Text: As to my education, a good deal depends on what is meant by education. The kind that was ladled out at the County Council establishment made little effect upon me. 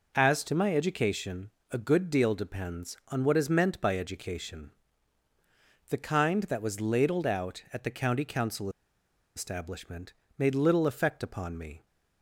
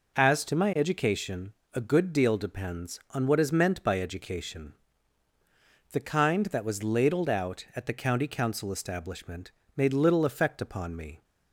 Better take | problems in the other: second | pauses between "Council" and "establishment"; noticeable; at 8.6 s; 0.67 s long // pauses between "establishment" and "made"; slight; at 10.1 s; 0.26 s long; slight in the second

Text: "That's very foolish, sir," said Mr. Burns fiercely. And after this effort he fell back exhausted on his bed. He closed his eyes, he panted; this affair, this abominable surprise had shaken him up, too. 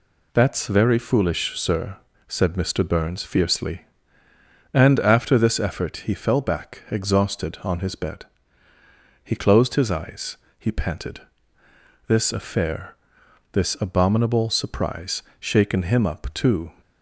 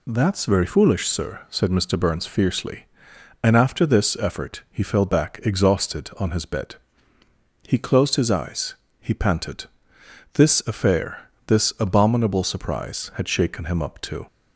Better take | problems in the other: second | skips "had"; at 15.3 s

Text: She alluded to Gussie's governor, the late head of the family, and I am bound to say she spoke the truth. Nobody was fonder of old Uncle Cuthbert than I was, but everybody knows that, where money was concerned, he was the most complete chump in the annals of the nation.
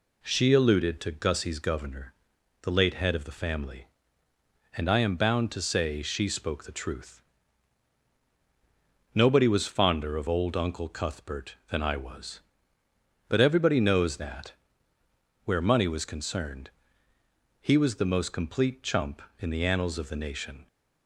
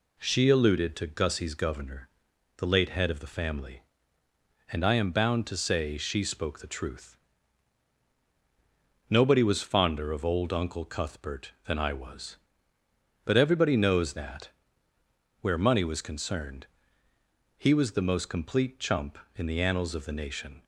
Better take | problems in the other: neither | none

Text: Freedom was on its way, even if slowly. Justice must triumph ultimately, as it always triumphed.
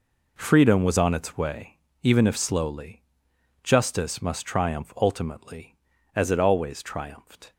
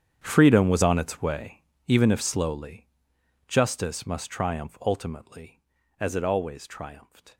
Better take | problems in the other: first | gets quieter; strong; throughout; 18.5 dB

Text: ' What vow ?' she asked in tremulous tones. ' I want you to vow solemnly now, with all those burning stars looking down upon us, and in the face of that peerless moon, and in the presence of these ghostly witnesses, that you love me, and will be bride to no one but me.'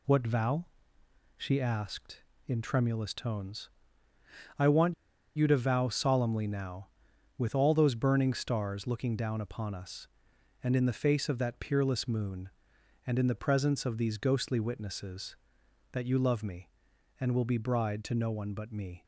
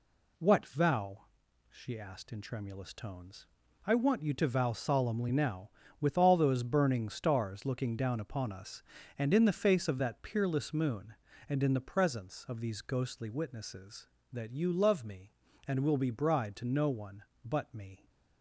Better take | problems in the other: second | pauses between "want" and "you"; at 4.9 s; 0.42 s long

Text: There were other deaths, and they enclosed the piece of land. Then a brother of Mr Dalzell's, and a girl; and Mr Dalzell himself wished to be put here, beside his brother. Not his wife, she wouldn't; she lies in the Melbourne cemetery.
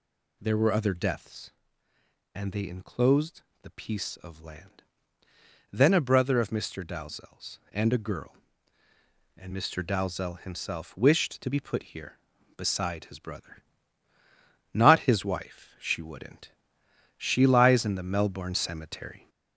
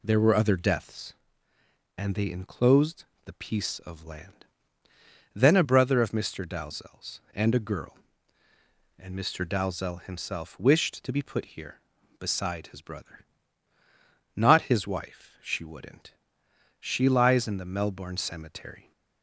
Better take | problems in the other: second | gets louder; throughout; 4 dB // pauses between "enclosed" and "the"; slight; at 3.4 s; 0.20 s long; slight in the second

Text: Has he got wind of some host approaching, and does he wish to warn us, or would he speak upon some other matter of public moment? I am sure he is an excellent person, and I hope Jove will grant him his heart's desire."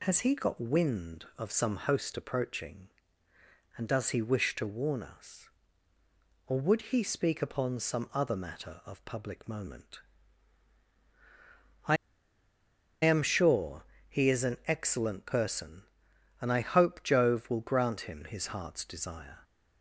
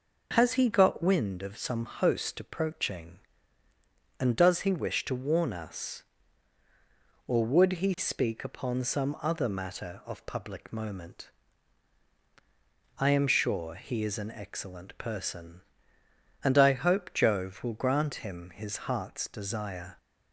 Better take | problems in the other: second | pauses between "I" and "am"; at 11.9 s; 1.0 s long // pauses between "sure" and "he"; slight; at 13.8 s; 0.22 s long

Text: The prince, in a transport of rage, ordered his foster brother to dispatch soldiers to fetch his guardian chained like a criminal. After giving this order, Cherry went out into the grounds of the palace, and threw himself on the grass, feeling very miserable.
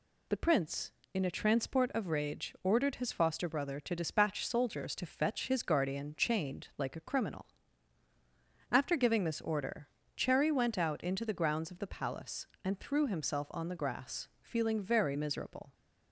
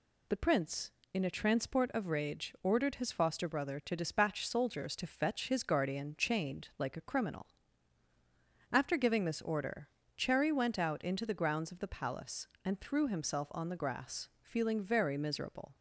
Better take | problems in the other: neither | none

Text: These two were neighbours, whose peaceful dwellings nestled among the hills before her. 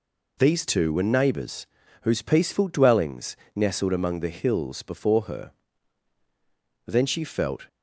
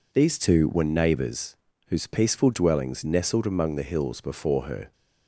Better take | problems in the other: second | pauses between "dwellings" and "nestled"; slight; at 3.3 s; 0.20 s long // goes on to say "Then she felt"; noticeable; from 6.8 s on; 0.82 s long

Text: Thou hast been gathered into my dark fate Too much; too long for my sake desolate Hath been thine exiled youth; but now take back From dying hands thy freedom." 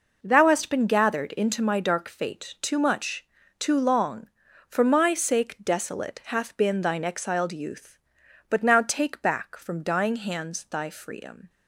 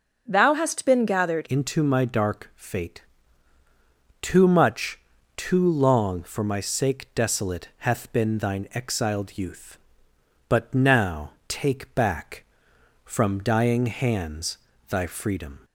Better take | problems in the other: first | changes voice at "into"; from 1.4 s on; 14.1 s long // pauses between "fate" and "Too"; at 2.9 s; 1.2 s long // pauses between "now" and "take"; slight; at 11.2 s; 0.18 s long // pauses between "hands" and "thy"; slight; at 14.5 s; 0.32 s long

